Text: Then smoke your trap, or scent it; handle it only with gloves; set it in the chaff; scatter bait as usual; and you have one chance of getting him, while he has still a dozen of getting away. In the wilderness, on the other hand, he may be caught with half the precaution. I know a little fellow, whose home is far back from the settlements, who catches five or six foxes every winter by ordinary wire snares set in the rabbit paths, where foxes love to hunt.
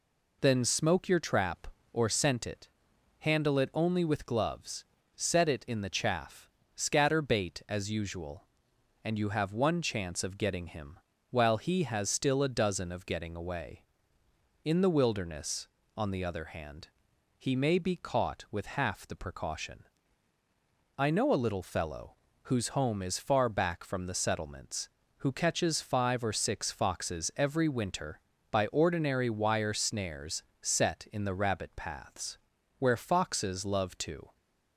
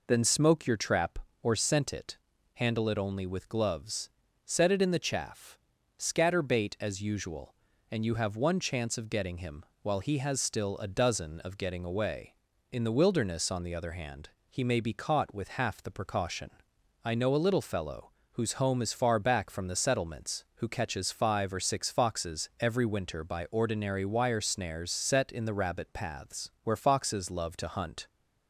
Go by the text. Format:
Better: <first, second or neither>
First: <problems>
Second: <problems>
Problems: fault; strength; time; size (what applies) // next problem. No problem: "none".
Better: second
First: pauses between "snares" and "set"; slight; at 30.4 s; 0.18 s long // stops before "hunt"; at 34.3 s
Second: none